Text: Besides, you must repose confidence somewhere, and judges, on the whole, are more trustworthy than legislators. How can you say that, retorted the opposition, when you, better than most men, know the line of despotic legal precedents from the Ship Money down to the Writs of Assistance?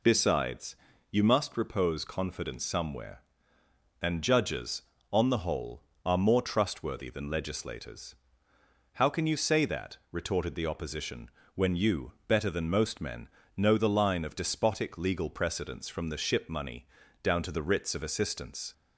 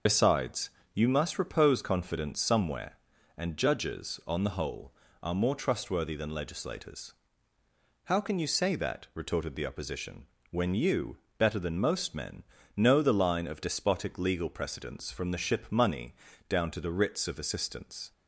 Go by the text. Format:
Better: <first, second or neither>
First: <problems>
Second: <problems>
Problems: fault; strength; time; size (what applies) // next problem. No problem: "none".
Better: first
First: pauses between "Money" and "down"; slight; at 16.8 s; 0.36 s long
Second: loses the start of "Besides"; at 0.0 s; 55 ms // pauses between "Money" and "down"; slight; at 16.1 s; 0.34 s long